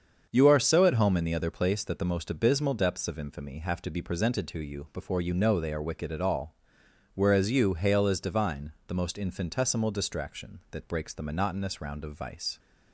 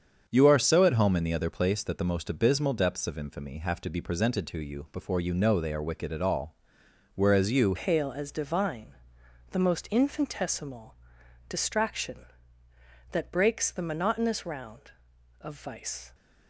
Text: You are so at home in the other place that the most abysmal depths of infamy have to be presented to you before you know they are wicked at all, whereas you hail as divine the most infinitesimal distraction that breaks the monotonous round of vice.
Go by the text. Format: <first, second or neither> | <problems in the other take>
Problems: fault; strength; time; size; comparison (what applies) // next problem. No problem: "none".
first | starts louder than the rest; until 1.3 s; 7 dB; also in the first // changes voice at "hail"; from 7.7 s on; 8.4 s long // pauses between "divine" and "the"; noticeable; at 8.9 s; 0.58 s long; slight in the first // pauses between "infinitesimal" and "distraction"; noticeable; at 10.9 s; 0.54 s long